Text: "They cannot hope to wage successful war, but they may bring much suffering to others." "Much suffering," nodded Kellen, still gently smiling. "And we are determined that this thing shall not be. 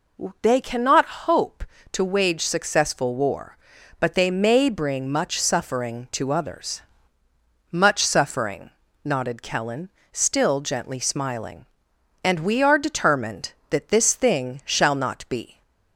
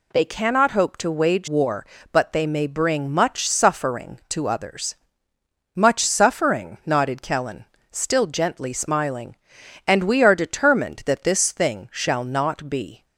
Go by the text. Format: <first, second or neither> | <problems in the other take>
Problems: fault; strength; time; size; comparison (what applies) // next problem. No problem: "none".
first | skips "successful"; at 1.4 s